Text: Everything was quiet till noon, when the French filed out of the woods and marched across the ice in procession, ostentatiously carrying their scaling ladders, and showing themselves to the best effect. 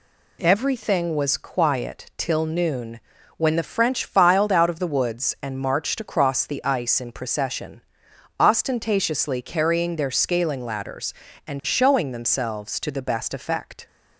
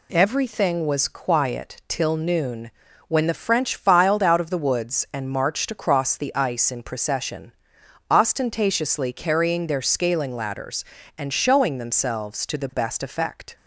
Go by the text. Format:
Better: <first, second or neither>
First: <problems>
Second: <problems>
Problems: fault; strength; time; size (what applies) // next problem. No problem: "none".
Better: neither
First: none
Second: none